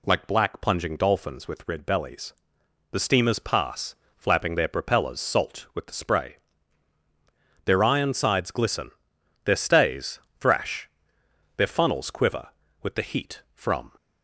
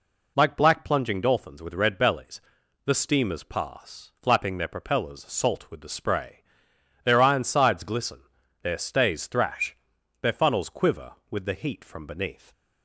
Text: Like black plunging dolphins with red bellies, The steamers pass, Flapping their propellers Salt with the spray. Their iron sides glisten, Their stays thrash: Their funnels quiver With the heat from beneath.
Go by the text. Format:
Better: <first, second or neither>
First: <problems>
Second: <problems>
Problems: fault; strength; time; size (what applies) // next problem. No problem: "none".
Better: second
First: pauses between "stays" and "thrash"; slight; at 10.1 s; 0.20 s long // stops before "beneath"; at 13.9 s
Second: none